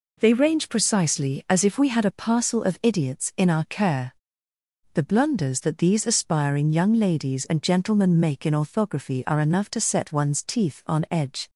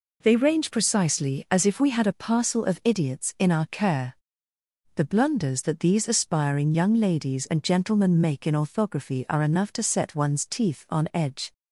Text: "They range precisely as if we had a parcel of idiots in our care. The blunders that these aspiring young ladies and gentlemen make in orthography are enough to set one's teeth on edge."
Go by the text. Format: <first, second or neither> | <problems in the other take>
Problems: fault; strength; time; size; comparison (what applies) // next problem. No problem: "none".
neither | none